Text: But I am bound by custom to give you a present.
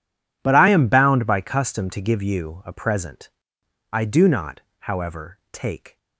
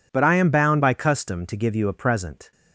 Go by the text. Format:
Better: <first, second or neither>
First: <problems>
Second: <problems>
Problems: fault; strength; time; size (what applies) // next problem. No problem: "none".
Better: second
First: goes on to say "I do not however take"; strong; from 3.9 s on; 2.0 s long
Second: none